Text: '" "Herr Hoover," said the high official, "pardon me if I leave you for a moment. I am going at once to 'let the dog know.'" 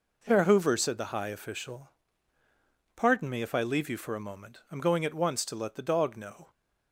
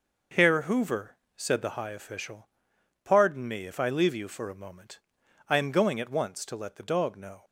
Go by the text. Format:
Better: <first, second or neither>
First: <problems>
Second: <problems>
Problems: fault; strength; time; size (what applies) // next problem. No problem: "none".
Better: neither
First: none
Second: none